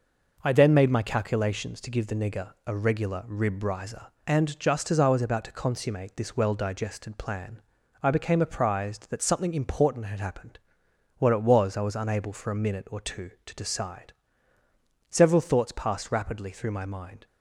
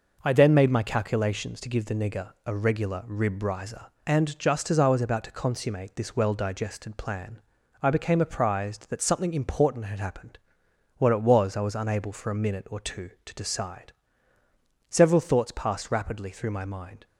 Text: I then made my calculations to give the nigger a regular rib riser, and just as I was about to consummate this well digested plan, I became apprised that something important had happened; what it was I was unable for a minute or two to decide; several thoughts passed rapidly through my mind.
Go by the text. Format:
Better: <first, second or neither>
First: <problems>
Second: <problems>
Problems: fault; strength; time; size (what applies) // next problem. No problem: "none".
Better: neither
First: none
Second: none